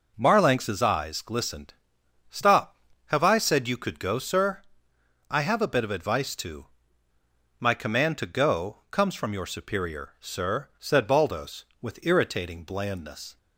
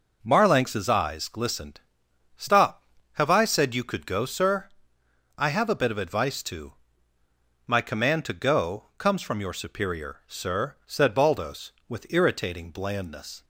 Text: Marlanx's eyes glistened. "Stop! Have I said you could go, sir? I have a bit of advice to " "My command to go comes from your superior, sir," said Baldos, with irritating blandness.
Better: neither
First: none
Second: none

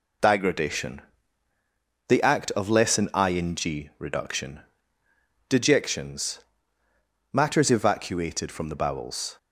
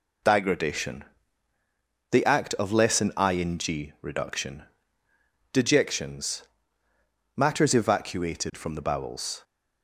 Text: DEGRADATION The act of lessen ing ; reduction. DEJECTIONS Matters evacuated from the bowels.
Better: neither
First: pauses between "DEGRADATION" and "The"; at 1.0 s; 1.0 s long // pauses between "DEJECTIONS" and "Matters"; noticeable; at 6.3 s; 0.94 s long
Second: pauses between "DEGRADATION" and "The"; at 1.0 s; 1.0 s long // pauses between "DEJECTIONS" and "Matters"; noticeable; at 6.4 s; 0.94 s long

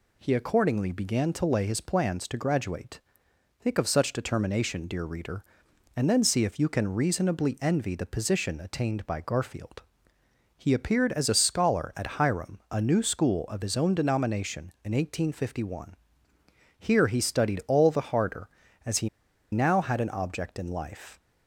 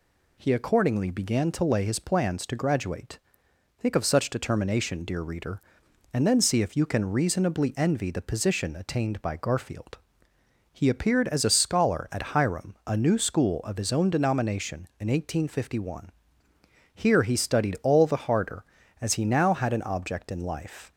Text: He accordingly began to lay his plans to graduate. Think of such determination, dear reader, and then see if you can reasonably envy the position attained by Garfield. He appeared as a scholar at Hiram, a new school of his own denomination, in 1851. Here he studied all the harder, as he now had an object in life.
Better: second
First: pauses between "he" and "now"; at 19.0 s; 0.43 s long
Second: none

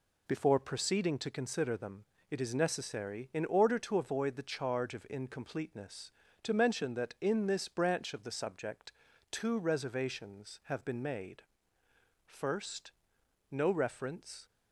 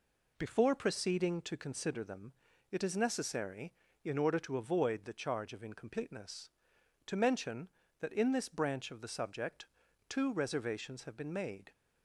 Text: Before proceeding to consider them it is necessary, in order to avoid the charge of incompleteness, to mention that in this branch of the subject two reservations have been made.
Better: second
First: pauses between "them" and "it"; slight; at 2.0 s; 0.26 s long // pauses between "subject" and "two"; at 8.9 s; 0.40 s long // goes on to say "First no reference"; strong; from 12.2 s on; 2.2 s long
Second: pauses between "them" and "it"; slight; at 2.3 s; 0.36 s long // pauses between "subject" and "two"; at 9.6 s; 0.44 s long

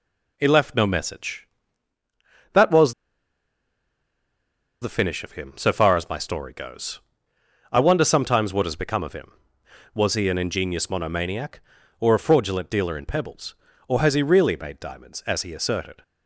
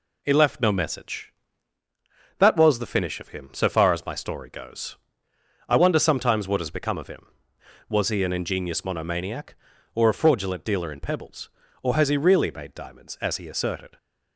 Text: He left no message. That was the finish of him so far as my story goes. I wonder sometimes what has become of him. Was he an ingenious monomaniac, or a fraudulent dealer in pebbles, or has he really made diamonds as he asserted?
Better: second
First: pauses between "was" and "the"; strong; at 2.9 s; 1.8 s long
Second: none

